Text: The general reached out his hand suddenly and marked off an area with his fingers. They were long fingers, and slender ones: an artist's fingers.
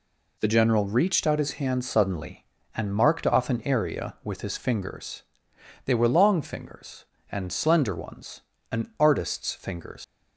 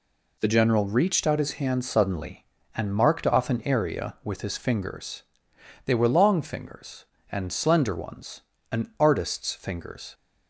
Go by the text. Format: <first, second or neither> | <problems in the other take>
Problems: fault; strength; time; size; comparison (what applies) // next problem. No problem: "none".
second | leaves "fingers" unfinished; at 10.0 s; 95 ms